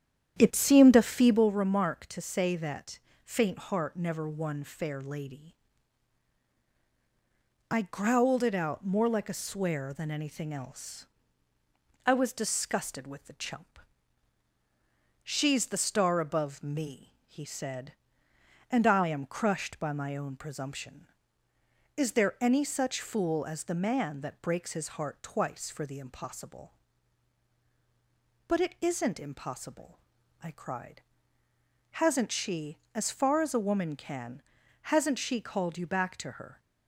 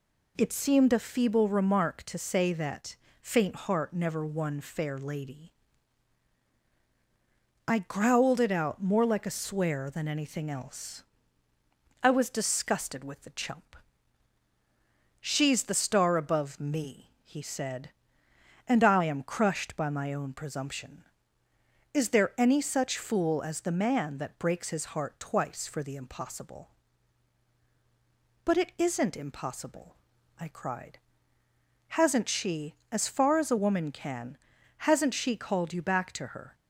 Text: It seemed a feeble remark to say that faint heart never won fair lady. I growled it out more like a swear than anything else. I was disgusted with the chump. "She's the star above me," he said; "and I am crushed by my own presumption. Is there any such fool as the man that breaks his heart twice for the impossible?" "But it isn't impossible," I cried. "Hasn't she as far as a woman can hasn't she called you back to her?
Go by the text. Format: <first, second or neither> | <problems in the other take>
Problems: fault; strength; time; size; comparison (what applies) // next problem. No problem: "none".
second | starts louder than the rest; strong; until 1.5 s; 9.5 dB // pauses between "that" and "faint"; slight; at 2.9 s; 0.26 s long; slight in the second // pauses between "can" and "hasn't"; at 34.4 s; 0.42 s long; also in the second